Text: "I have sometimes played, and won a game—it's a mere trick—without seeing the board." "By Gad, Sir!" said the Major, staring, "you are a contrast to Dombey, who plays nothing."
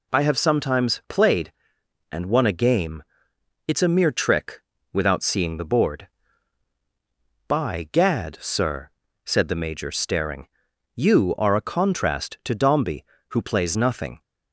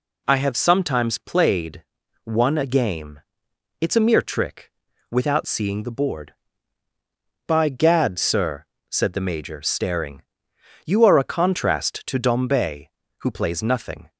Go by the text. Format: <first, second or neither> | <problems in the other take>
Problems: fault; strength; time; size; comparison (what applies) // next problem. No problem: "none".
first | skips "and"; at 2.0 s